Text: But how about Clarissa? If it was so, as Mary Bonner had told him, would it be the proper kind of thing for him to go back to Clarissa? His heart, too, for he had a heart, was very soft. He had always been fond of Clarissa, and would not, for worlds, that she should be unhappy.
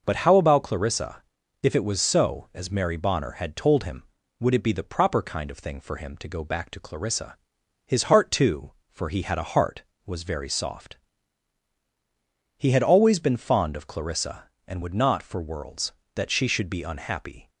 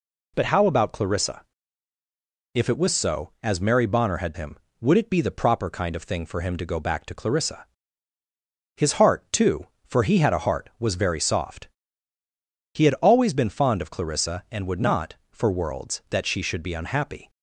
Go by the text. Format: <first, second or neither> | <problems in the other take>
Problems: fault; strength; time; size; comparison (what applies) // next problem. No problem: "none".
first | skips "told"; at 4.3 s